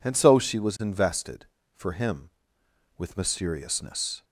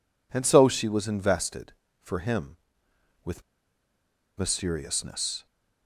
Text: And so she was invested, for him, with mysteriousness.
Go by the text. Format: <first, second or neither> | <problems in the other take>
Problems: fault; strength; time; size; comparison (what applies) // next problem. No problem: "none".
first | pauses between "with" and "mysteriousness"; noticeable; at 3.4 s; 0.95 s long